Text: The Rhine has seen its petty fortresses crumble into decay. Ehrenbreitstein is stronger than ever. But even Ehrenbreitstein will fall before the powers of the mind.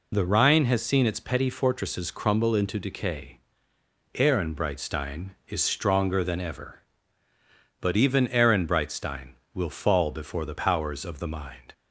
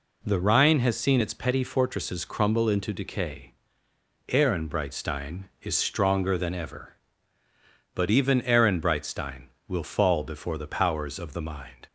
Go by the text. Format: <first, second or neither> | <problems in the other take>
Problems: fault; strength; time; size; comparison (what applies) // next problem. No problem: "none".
second | loses the start of "The"; at 0.1 s; 35 ms